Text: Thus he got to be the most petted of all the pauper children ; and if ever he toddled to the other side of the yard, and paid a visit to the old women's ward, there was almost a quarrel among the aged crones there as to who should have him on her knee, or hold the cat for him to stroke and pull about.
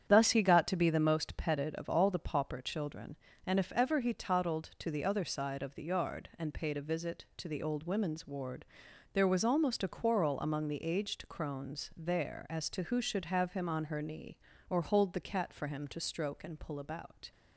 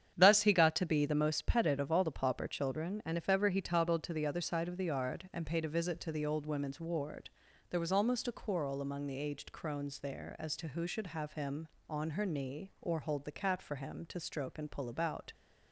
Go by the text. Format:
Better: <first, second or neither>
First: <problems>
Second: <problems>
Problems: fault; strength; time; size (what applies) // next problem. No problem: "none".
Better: neither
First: starts louder than the rest; strong; until 1.0 s; 9 dB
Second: starts louder than the rest; strong; until 1.1 s; 8.5 dB